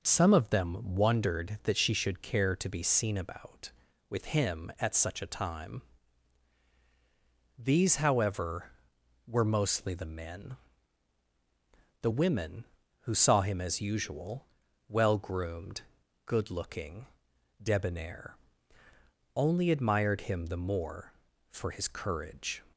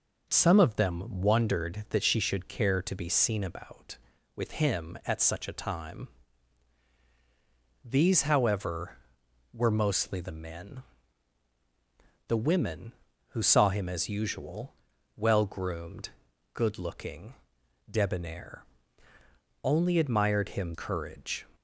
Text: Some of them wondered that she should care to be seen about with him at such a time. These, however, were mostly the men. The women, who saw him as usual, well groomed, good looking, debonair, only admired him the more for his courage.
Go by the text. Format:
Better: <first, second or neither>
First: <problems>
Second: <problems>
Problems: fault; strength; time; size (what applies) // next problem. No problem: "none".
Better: first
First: none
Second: skips "the more for his"; at 20.7 s